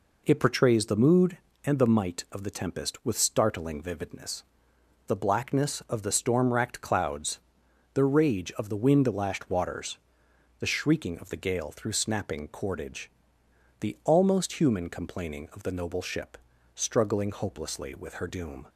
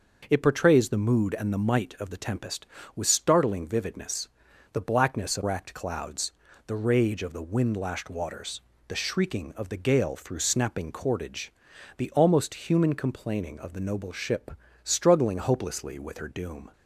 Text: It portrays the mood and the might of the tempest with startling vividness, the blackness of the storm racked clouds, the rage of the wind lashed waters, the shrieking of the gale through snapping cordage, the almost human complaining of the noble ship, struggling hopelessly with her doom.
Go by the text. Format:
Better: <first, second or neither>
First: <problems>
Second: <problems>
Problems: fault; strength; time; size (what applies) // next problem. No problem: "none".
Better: first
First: none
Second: skips "the storm"; at 5.4 s